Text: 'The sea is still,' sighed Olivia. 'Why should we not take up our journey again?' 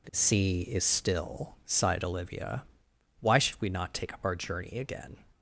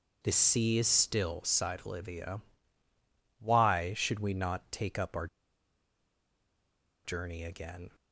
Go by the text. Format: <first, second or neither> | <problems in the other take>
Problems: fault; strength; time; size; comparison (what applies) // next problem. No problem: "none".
first | pauses between "our" and "journey"; strong; at 5.2 s; 1.7 s long